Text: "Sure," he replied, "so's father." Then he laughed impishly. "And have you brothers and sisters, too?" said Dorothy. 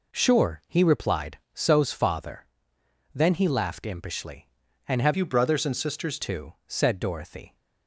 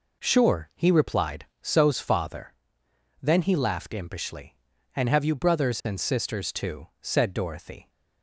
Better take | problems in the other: second | changes voice from "you" to "sisters"; from 5.1 to 6.1 s; 1.0 s long

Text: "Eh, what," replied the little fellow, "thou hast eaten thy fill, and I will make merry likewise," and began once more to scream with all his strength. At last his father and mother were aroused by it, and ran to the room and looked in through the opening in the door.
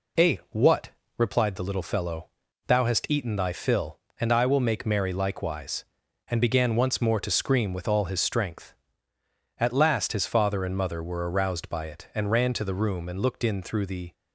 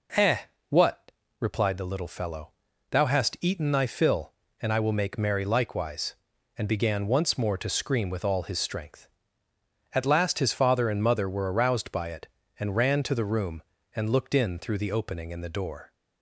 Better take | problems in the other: second | stops before "opening in the door"; at 14.1 s

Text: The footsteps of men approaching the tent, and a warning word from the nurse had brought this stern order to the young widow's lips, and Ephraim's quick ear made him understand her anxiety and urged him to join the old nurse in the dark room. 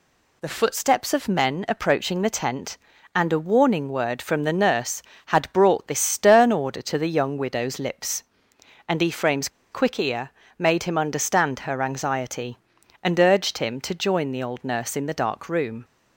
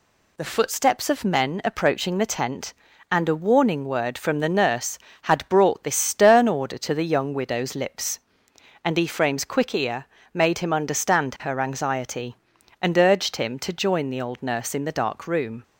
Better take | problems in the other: second | pauses between "Ephraim's" and "quick"; slight; at 9.4 s; 0.23 s long // pauses between "ear" and "made"; slight; at 10.3 s; 0.26 s long; slight in the second

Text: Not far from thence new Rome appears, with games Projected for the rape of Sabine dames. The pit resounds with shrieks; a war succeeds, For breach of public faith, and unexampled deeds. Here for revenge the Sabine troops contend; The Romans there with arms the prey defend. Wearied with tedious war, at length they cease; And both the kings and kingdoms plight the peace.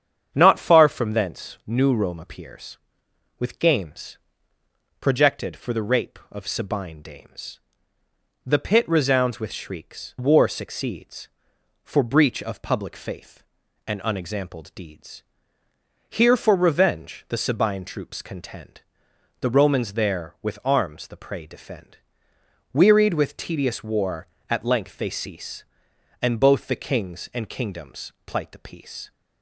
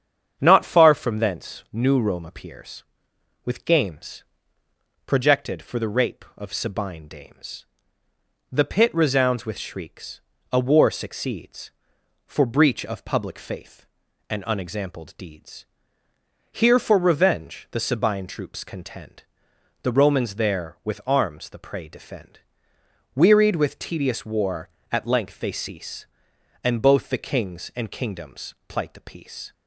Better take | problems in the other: second | starts louder than the rest; strong; until 1.3 s; 8 dB; strong in the second // pauses between "games" and "Projected"; noticeable; at 4.1 s; 0.84 s long; noticeable in the second // skips "a"; at 10.1 s // pauses between "kingdoms" and "plight"; slight; at 28.1 s; 0.16 s long; slight in the second

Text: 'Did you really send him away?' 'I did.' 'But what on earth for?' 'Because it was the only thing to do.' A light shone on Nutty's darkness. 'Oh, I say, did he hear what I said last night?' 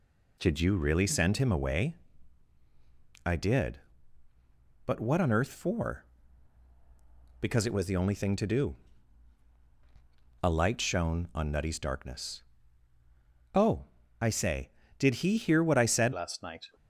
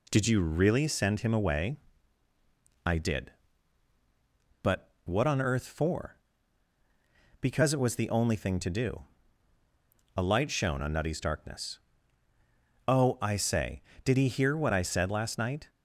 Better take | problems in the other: second | changes voice at "last"; from 16.1 s on; 0.5 s long

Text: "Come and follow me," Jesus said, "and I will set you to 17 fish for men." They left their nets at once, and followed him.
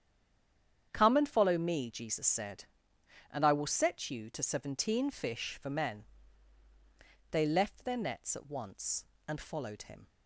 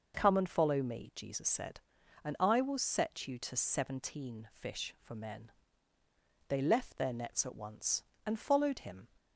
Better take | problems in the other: second | stays silent before the first word; slight; until 0.9 s; 0.9 s long // starts louder than the rest; strong; until 1.9 s; 8.5 dB

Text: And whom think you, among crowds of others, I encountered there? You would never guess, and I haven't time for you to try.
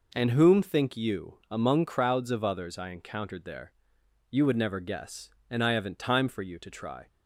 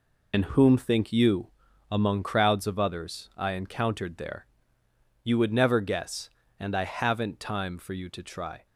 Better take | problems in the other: first | loses the start of "And"; at 0.3 s; 65 ms

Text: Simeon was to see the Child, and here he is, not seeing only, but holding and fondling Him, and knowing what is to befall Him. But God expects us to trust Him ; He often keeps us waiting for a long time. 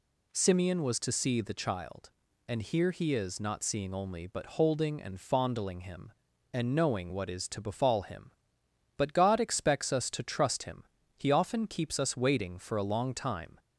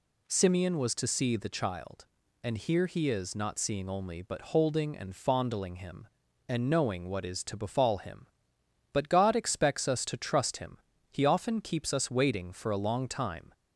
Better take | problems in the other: neither | none

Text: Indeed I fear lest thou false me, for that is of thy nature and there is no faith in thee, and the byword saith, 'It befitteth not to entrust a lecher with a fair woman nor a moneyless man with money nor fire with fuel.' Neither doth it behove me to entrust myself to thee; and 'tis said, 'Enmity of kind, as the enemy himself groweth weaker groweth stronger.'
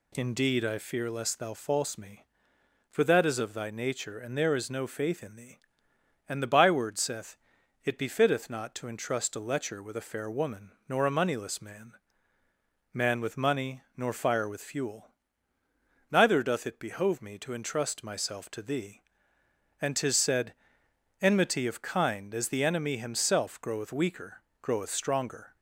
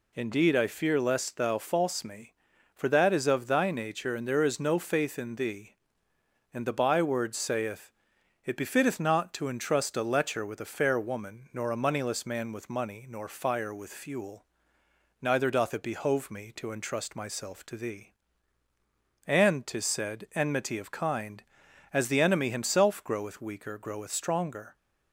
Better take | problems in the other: second | pauses between "woman" and "nor"; slight; at 10.7 s; 0.16 s long // says "man" twice; at 12.9 s // pauses between "money" and "nor"; slight; at 13.8 s; 0.16 s long // pauses between "weaker" and "groweth"; slight; at 24.4 s; 0.18 s long

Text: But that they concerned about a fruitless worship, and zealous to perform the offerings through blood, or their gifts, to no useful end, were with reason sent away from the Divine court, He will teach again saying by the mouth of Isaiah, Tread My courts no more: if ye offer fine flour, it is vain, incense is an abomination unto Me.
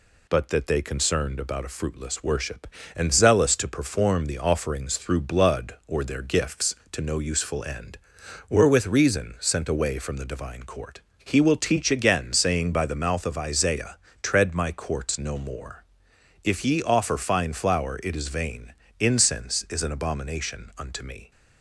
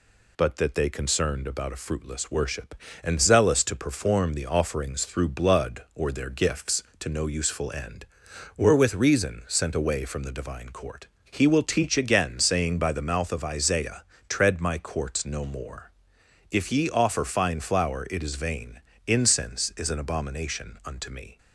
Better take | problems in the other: neither | none

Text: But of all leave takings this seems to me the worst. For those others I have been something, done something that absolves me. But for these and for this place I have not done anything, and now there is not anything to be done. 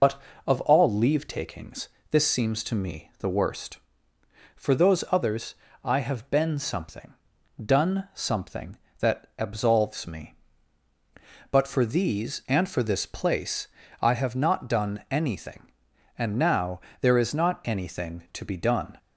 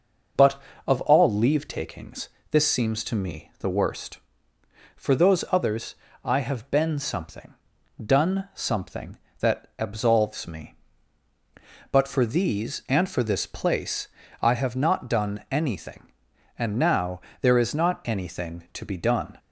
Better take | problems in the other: second | loses the start of "But"; at 0.0 s; 60 ms // pauses between "takings" and "this"; slight; at 1.8 s; 0.22 s long; slight in the second // pauses between "others" and "I"; slight; at 5.5 s; 0.30 s long; slight in the second // pauses between "place" and "I"; slight; at 13.6 s; 0.32 s long; slight in the second // pauses between "now" and "there"; slight; at 16.8 s; 0.20 s long; slight in the second

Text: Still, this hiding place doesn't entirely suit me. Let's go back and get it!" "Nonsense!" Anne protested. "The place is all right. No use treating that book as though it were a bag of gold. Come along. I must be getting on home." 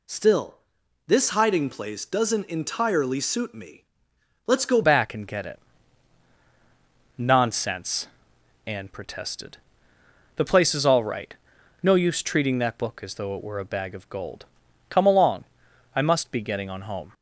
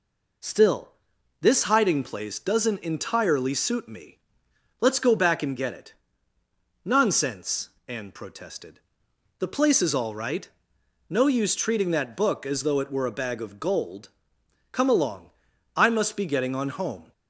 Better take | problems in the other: second | changes voice at "back"; from 4.8 s on; 12.3 s long

